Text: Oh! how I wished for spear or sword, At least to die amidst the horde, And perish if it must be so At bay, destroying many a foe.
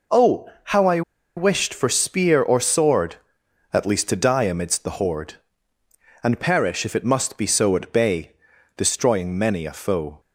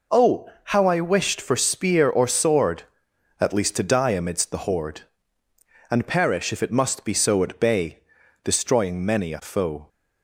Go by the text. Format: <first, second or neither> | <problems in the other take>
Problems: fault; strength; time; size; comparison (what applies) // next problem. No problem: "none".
second | pauses between "I" and "wished"; slight; at 1.0 s; 0.35 s long